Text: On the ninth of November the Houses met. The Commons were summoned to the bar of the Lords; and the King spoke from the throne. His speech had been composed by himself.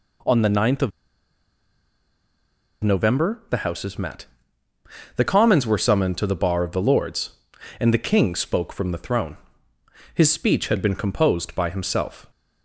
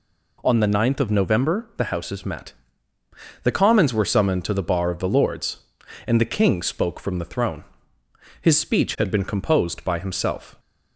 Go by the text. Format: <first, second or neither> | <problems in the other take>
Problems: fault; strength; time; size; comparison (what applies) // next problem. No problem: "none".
second | pauses between "of" and "November"; strong; at 0.9 s; 1.9 s long